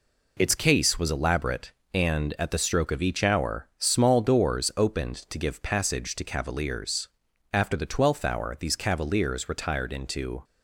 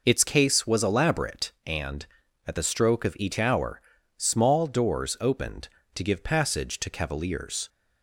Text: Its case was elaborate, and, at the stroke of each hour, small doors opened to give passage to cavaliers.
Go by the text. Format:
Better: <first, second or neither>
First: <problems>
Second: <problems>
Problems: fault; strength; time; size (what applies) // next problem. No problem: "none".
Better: second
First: goes on to say "After the twelfth hour these cavaliers retired into"; strong; from 7.5 s on; 2.9 s long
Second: none